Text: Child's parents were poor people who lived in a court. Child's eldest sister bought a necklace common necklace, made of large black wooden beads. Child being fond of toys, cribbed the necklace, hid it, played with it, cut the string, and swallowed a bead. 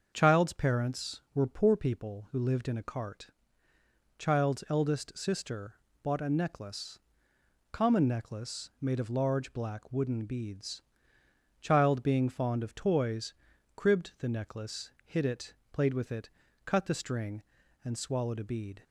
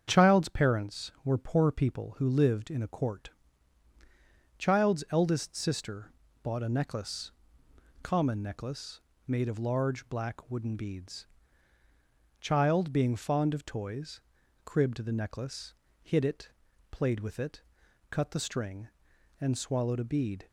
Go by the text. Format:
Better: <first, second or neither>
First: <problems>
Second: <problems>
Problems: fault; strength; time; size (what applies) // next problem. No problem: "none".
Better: second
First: starts louder than the rest; until 1.1 s; 6.5 dB // says "cart" for "court"; at 2.8 s // pauses between "sister" and "bought"; slight; at 5.7 s; 0.28 s long // pauses between "necklace" and "common"; noticeable; at 6.9 s; 0.72 s long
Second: starts louder than the rest; strong; until 1.0 s; 7.5 dB // pauses between "sister" and "bought"; slight; at 6.1 s; 0.30 s long // pauses between "necklace" and "common"; noticeable; at 7.3 s; 0.70 s long